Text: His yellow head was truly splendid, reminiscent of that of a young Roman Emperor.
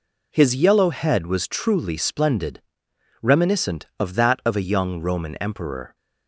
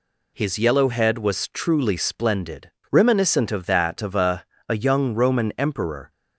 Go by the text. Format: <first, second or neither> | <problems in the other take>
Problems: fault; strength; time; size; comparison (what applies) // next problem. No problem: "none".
first | says "a" twice; at 4.6 s